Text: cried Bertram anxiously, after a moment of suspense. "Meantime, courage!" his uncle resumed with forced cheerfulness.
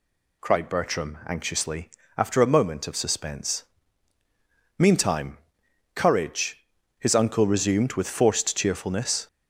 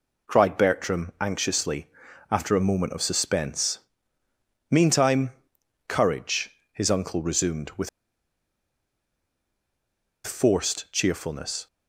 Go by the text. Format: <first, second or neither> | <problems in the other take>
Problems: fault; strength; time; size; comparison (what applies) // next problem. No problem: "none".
first | pauses between "with" and "forced"; strong; at 7.8 s; 2.3 s long